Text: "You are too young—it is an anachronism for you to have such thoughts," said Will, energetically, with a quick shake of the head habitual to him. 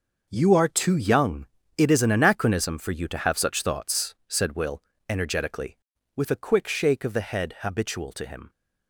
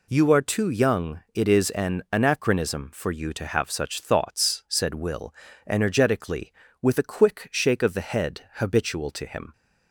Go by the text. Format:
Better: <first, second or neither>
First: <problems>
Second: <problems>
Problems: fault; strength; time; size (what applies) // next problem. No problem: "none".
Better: neither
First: none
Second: none